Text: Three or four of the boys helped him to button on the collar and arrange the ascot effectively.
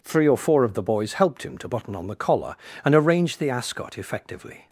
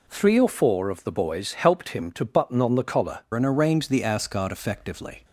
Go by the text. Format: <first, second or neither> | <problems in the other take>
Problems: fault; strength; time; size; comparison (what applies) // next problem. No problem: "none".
first | changes voice at "and"; from 3.3 s on; 1.9 s long